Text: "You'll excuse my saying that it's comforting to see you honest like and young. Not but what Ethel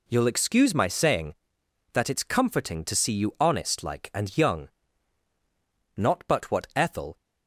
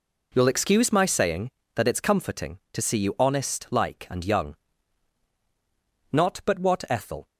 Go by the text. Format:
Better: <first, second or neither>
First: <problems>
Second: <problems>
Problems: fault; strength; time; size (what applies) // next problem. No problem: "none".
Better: neither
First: none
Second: none